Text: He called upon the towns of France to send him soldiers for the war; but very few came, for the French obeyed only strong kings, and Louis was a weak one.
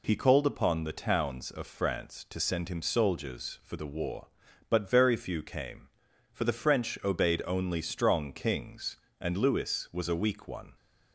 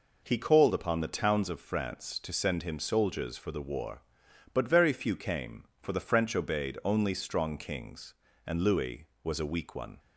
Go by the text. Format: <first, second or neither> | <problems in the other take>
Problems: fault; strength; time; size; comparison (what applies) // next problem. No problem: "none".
neither | none